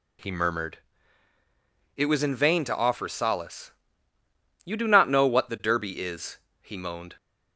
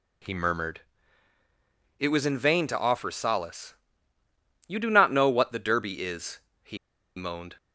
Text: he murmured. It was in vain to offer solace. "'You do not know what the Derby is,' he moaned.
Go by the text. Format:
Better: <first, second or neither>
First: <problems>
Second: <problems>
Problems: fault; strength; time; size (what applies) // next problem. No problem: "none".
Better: first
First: none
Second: pauses between "he" and "moaned"; at 6.7 s; 0.40 s long